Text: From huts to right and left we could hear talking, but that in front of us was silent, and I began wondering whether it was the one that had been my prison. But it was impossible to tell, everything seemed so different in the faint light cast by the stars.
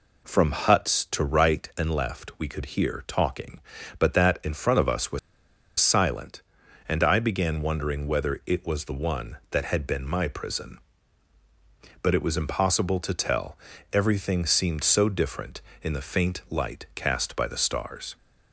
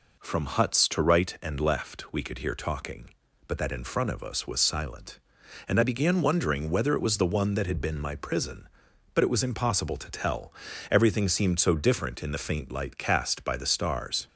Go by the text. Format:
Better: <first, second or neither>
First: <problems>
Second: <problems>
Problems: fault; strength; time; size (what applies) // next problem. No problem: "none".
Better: second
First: pauses between "was" and "silent"; noticeable; at 5.1 s; 0.60 s long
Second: none